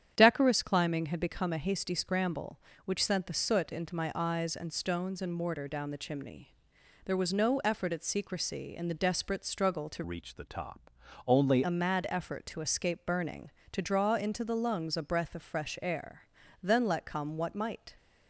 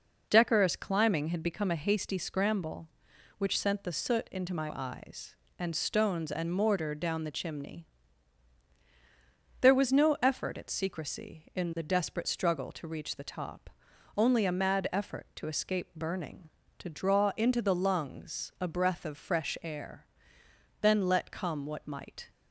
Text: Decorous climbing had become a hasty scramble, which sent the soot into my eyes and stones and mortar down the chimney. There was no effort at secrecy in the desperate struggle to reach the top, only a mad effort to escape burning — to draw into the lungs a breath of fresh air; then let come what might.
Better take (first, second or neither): second